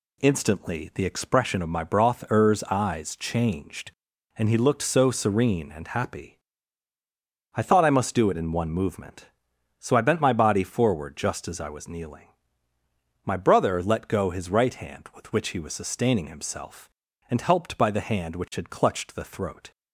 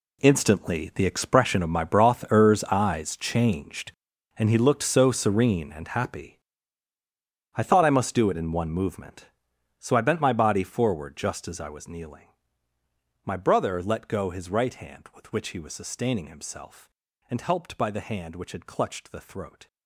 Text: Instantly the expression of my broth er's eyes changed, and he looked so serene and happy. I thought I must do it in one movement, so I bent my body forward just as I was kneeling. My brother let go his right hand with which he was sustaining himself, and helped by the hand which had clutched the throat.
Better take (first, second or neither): first